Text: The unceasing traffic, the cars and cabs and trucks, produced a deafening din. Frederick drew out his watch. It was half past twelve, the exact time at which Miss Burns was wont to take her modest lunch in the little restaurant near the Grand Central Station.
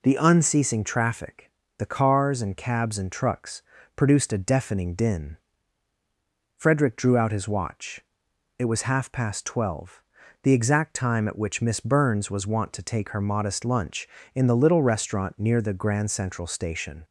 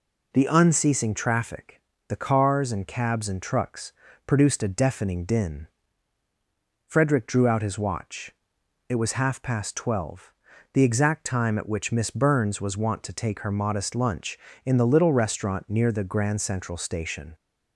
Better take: neither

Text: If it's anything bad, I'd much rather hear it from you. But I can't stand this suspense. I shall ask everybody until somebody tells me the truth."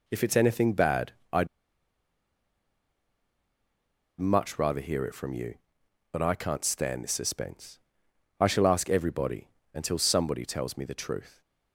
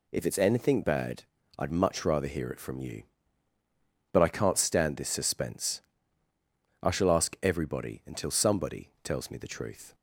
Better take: second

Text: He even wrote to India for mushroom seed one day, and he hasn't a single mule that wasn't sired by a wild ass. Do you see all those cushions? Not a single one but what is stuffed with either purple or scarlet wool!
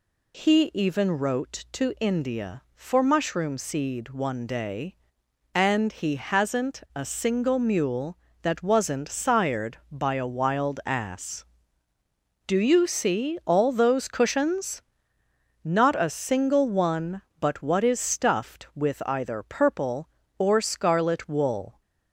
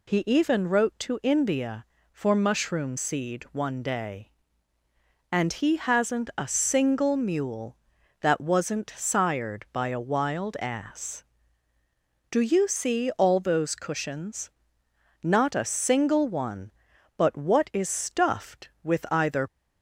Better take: first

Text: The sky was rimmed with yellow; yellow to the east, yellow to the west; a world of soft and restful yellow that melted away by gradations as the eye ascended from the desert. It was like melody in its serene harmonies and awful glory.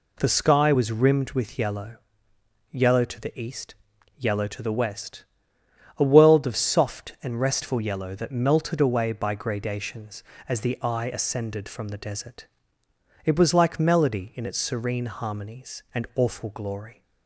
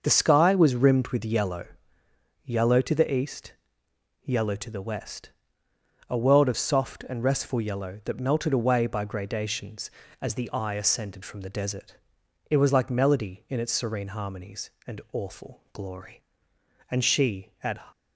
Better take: first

